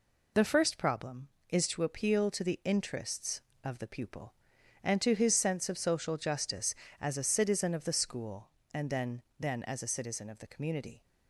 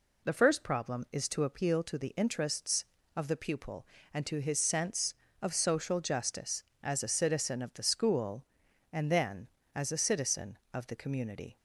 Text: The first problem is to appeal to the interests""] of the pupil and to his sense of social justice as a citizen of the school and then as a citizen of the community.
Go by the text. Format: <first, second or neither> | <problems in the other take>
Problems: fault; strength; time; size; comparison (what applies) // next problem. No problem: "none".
second | says "then" twice; at 9.3 s